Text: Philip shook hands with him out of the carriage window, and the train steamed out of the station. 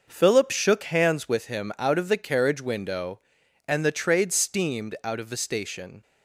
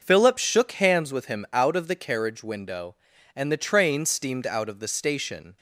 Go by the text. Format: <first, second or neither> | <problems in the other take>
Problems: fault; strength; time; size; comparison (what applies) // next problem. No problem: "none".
second | says "trade" for "train"; at 3.9 s